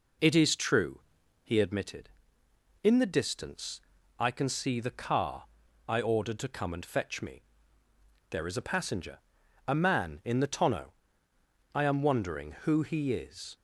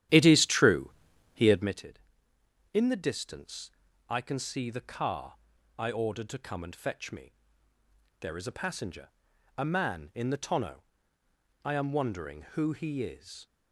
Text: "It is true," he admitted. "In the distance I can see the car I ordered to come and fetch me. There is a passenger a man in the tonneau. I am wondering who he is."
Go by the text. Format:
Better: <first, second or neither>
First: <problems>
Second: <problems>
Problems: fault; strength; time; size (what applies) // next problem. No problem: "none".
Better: first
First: pauses between "distance" and "I"; at 3.7 s; 0.40 s long // pauses between "car" and "I"; at 5.4 s; 0.42 s long // pauses between "passenger" and "a"; noticeable; at 9.1 s; 0.46 s long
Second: starts louder than the rest; strong; until 1.9 s; 11.5 dB // pauses between "distance" and "I"; at 3.6 s; 0.40 s long // pauses between "car" and "I"; at 5.3 s; 0.42 s long // pauses between "passenger" and "a"; noticeable; at 9.0 s; 0.46 s long